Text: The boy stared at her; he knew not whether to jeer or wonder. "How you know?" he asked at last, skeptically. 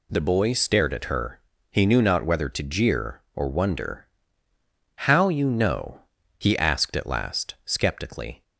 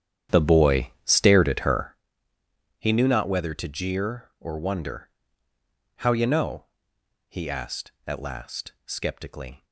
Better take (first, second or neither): first